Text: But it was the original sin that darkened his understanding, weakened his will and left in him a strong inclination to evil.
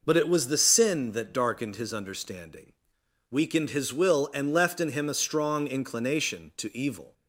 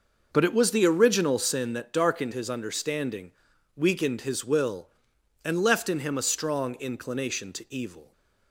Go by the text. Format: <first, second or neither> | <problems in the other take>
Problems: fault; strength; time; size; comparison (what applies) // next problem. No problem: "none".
second | skips "original"; at 0.5 s